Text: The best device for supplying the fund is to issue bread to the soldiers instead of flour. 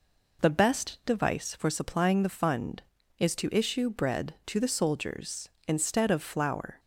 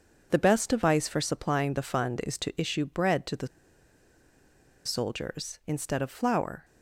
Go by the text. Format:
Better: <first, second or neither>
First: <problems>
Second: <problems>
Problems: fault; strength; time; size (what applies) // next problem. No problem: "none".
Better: first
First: none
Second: pauses between "the" and "soldiers"; strong; at 3.4 s; 1.3 s long